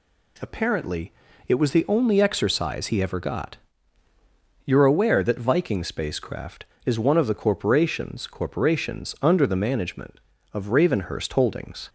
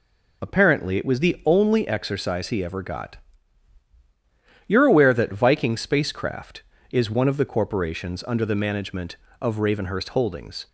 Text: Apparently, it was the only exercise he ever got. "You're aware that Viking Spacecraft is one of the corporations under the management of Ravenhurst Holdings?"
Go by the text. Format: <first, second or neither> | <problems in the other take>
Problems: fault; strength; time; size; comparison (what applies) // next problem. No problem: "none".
second | says "corporations" twice; at 8.2 s